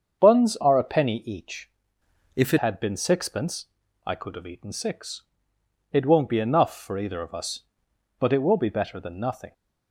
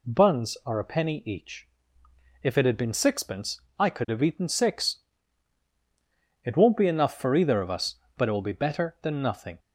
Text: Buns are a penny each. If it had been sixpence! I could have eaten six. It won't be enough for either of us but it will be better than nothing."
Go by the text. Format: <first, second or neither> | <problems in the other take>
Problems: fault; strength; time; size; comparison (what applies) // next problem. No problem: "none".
second | starts louder than the rest; until 1.3 s; 7 dB // changes voice from "If" to "it"; from 2.3 to 2.5 s; 0.2 s long